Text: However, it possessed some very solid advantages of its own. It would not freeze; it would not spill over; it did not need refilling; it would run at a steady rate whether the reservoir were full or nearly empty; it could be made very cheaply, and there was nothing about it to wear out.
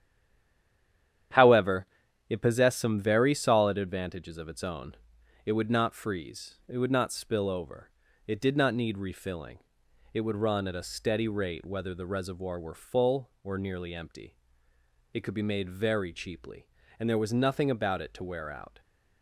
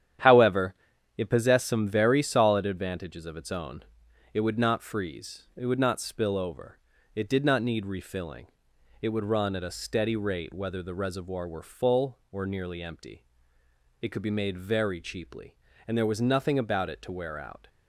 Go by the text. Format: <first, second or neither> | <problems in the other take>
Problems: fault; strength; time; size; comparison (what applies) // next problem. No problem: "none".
second | stays silent before the first word; noticeable; until 1.3 s; 1.3 s long // starts louder than the rest; strong; until 2.7 s; 10 dB; strong in the second